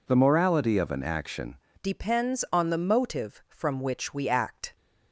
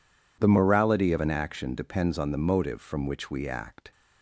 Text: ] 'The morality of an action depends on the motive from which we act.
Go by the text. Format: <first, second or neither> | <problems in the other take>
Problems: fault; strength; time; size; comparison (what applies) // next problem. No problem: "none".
second | changes voice at "depends"; from 1.8 s on; 2.9 s long